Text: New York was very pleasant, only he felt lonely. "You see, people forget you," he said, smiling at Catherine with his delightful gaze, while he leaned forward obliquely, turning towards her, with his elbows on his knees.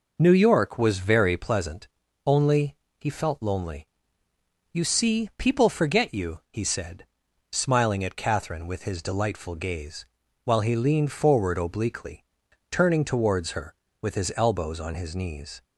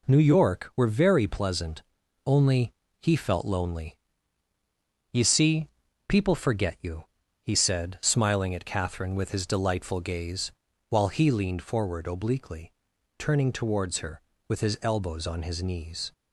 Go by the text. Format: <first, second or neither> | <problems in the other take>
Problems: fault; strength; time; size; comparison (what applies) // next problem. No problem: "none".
first | says "were" for "was"; at 0.7 s // pauses between "only" and "he"; slight; at 2.7 s; 0.26 s long; slight in the first